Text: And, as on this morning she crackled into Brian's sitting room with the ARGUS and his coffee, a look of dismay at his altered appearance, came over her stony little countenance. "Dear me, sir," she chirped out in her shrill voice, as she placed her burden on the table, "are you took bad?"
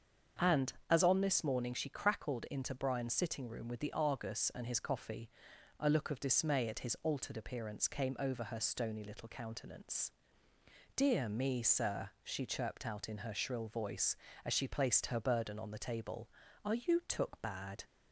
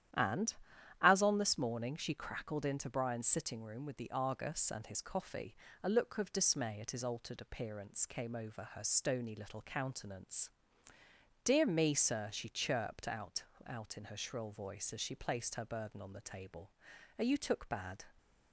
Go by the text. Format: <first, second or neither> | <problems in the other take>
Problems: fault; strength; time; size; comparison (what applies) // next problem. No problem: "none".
first | starts louder than the rest; strong; until 1.6 s; 11 dB; also in the first // says "out" twice; at 13.6 s